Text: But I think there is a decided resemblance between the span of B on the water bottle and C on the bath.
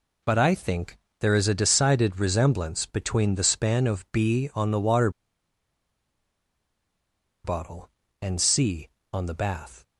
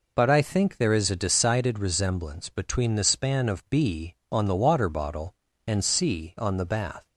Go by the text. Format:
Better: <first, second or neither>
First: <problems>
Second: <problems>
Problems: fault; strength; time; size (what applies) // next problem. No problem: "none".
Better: second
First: pauses between "think" and "there"; slight; at 0.9 s; 0.24 s long // pauses between "water" and "bottle"; strong; at 5.1 s; 2.3 s long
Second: none